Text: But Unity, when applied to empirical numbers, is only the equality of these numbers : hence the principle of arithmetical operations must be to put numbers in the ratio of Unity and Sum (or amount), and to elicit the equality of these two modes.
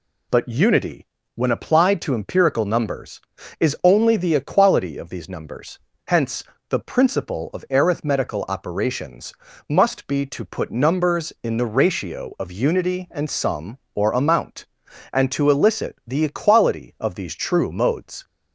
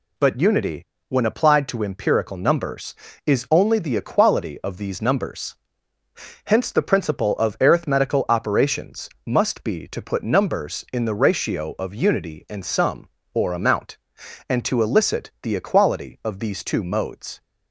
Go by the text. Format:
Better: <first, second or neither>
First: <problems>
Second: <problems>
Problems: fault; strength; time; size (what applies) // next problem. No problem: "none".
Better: second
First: pauses between "hence" and "the"; slight; at 6.4 s; 0.26 s long // pauses between "operations" and "must"; slight; at 9.3 s; 0.34 s long // says "true" for "two"; at 17.3 s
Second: pauses between "operations" and "must"; slight; at 9.1 s; 0.16 s long